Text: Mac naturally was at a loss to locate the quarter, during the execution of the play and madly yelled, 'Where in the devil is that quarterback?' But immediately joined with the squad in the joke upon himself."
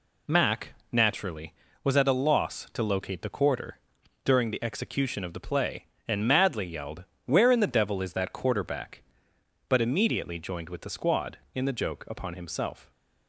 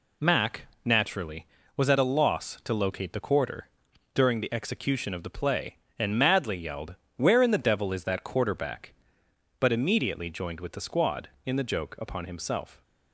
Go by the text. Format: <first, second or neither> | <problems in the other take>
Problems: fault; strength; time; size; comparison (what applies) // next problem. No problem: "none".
neither | pauses between "Mac" and "naturally"; slight; the same in both